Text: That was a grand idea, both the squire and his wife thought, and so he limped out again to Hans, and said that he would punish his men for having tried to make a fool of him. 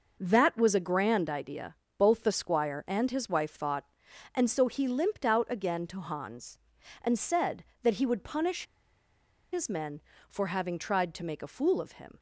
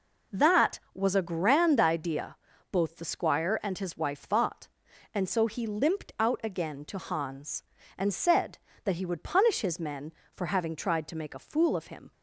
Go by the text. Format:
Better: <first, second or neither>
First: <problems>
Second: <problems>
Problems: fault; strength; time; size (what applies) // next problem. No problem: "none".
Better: second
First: pauses between "punish" and "his"; noticeable; at 8.6 s; 0.88 s long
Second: none